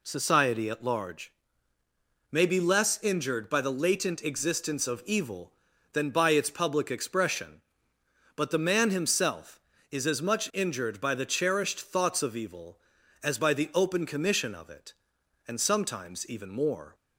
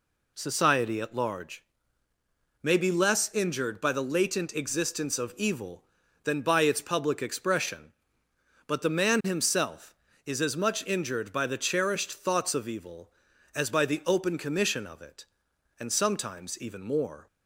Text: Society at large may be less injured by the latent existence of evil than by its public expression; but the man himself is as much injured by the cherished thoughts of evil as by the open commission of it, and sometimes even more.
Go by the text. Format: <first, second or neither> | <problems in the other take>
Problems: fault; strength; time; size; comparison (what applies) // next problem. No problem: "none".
neither | pauses between "large" and "may"; noticeable; the same in both